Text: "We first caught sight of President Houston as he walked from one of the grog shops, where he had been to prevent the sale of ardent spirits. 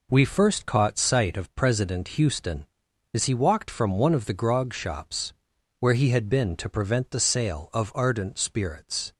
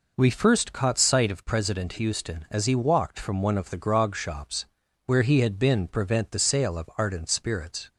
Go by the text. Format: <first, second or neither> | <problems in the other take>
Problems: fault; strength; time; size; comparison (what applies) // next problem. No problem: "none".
first | skips "to"; at 5.8 s